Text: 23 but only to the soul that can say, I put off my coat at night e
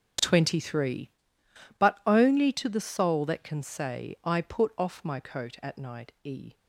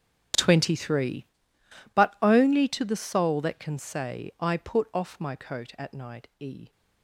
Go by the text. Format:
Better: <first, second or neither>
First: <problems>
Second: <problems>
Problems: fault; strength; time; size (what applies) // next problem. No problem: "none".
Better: first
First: starts louder than the rest; strong; until 1.9 s; 8.5 dB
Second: gets quieter; strong; throughout; 19 dB // starts louder than the rest; strong; until 2.0 s; 10 dB